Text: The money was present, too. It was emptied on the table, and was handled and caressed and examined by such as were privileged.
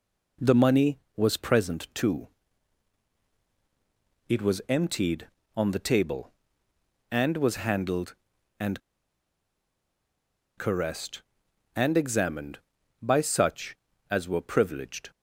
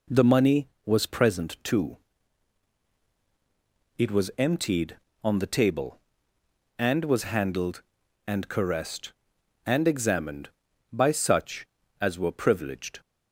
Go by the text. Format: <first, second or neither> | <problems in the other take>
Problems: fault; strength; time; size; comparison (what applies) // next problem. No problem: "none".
second | pauses between "and" and "caressed"; strong; at 8.7 s; 1.7 s long